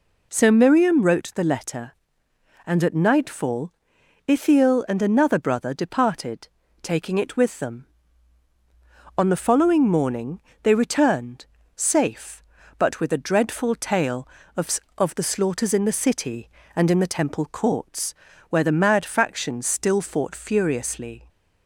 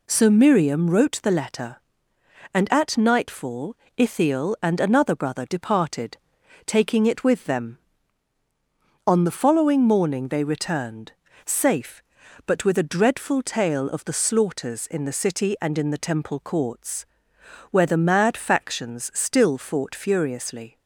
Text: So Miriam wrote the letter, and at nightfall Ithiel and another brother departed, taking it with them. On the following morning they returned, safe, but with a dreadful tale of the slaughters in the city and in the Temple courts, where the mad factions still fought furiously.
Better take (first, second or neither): second